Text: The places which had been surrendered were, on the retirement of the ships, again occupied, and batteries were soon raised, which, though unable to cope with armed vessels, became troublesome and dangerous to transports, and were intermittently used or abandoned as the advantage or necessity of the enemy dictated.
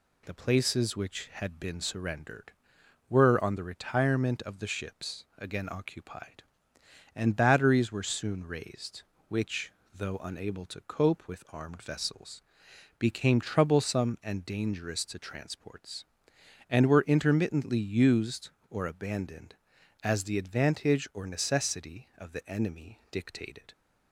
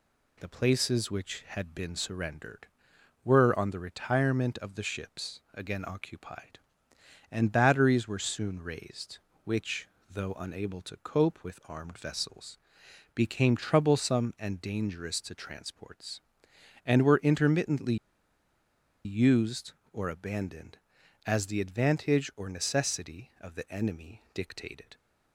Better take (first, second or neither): first